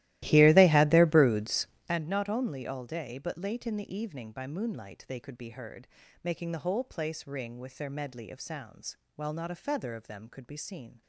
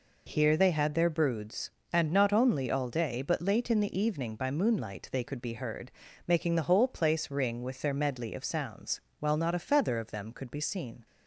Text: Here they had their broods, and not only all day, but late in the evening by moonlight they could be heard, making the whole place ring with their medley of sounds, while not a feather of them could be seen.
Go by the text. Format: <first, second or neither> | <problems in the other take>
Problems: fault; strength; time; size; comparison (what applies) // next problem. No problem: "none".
second | starts louder than the rest; strong; until 2.0 s; 16 dB